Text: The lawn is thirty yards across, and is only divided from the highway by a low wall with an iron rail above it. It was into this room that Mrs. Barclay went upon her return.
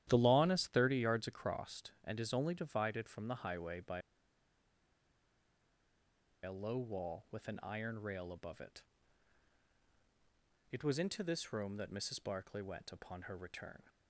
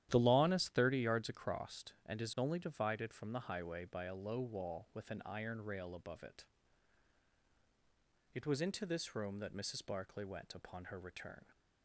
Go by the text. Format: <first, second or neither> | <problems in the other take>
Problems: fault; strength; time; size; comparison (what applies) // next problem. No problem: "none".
second | starts louder than the rest; strong; until 1.0 s; 11.5 dB; strong in the second // pauses between "by" and "a"; strong; at 4.0 s; 2.4 s long